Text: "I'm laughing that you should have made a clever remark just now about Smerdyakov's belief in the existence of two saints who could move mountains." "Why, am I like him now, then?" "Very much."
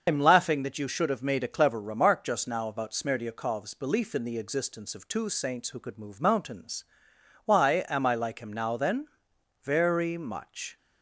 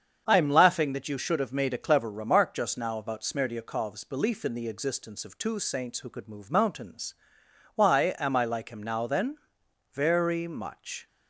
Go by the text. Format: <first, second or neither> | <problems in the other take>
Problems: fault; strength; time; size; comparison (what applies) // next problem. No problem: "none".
second | loses the start of "I'm"; at 0.0 s; 105 ms // starts louder than the rest; until 1.0 s; 6 dB; strong in the second